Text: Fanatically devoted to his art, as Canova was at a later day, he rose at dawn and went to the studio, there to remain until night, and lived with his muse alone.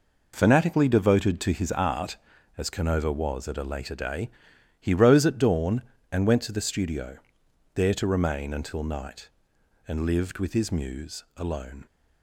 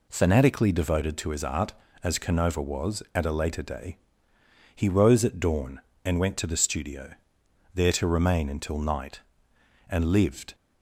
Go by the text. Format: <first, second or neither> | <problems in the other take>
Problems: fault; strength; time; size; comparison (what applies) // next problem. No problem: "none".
first | stops before "with his muse alone"; at 10.5 s